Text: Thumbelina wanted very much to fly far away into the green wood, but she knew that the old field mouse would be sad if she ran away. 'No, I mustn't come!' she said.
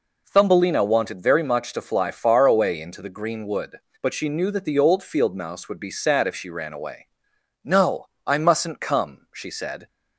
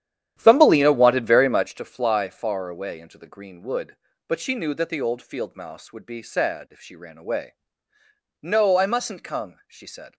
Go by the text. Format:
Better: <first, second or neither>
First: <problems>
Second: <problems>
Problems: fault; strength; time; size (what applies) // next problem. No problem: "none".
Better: first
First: none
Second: starts louder than the rest; strong; until 1.8 s; 10.5 dB